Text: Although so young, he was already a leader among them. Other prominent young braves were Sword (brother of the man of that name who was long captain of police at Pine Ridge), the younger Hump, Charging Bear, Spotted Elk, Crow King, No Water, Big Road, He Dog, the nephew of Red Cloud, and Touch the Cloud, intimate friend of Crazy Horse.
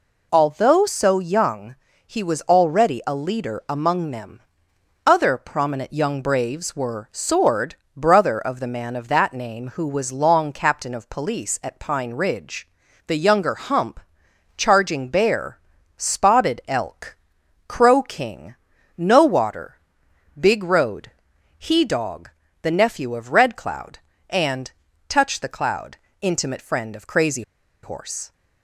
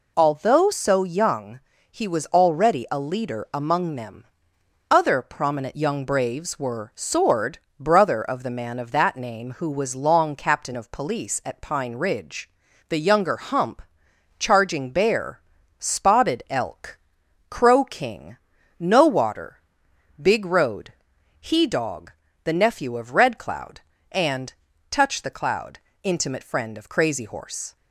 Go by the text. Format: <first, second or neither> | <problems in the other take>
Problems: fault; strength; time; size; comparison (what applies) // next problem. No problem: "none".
second | pauses between "and" and "Touch"; at 24.6 s; 0.38 s long; also in the second // pauses between "Crazy" and "Horse"; at 27.4 s; 0.41 s long